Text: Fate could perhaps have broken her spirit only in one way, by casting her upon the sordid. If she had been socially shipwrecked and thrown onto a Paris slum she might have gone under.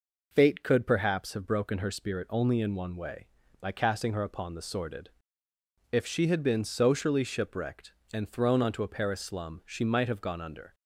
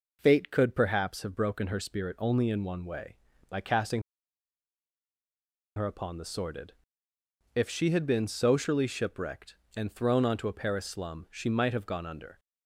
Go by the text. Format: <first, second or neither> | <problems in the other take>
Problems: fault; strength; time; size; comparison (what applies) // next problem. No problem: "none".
first | pauses between "casting" and "her"; strong; at 4.0 s; 1.7 s long